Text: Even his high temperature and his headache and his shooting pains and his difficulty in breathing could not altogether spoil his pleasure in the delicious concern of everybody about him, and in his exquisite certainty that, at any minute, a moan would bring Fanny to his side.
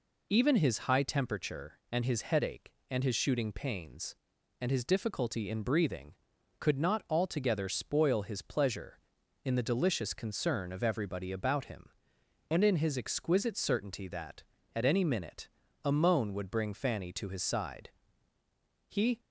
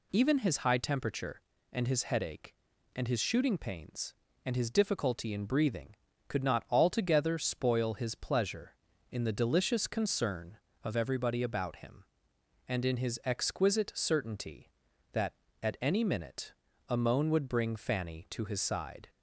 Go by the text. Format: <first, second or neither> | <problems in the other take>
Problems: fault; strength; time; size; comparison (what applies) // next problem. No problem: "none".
second | goes on to say "He"; slight; from 18.8 s on; 0.32 s long